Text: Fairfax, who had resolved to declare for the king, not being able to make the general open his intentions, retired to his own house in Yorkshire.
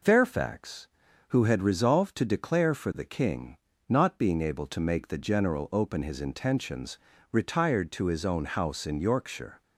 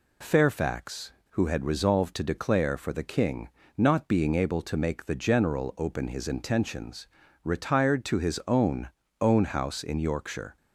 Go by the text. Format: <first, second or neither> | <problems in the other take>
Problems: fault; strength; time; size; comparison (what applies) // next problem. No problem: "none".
first | says "own" twice; at 9.2 s